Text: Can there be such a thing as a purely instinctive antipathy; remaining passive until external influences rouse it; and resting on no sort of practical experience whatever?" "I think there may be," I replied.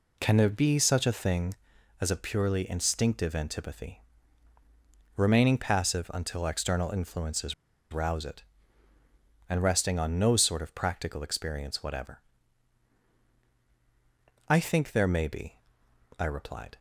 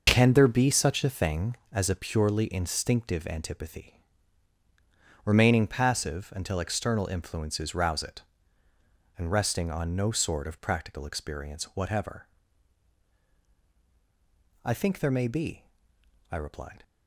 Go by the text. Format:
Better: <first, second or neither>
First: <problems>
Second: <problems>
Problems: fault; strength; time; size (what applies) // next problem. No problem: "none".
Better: second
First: pauses between "influences" and "rouse"; at 7.5 s; 0.36 s long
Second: none